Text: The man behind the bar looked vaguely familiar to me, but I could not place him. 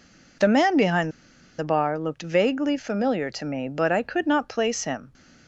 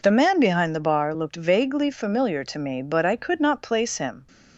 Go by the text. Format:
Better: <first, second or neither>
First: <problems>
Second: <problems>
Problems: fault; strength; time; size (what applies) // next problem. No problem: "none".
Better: second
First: pauses between "behind" and "the"; noticeable; at 1.1 s; 0.48 s long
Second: none